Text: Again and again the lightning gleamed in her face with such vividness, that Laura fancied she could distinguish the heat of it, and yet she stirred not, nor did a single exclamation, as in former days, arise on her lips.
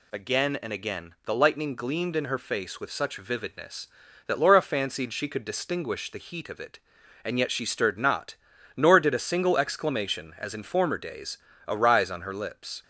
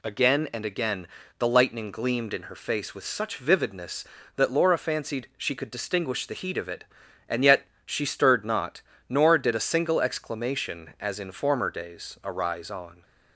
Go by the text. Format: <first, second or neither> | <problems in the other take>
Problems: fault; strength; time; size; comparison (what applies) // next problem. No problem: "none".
first | pauses between "again" and "the"; slight; at 1.0 s; 0.32 s long // pauses between "yet" and "she"; slight; at 7.6 s; 0.20 s long // stops before "her lips"; at 13.0 s